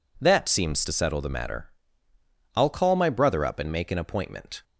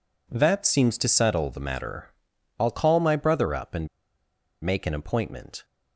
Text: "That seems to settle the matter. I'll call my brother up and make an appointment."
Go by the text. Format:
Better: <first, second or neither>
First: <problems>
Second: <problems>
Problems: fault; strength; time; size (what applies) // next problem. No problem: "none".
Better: first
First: none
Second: pauses between "and" and "make"; noticeable; at 3.8 s; 0.74 s long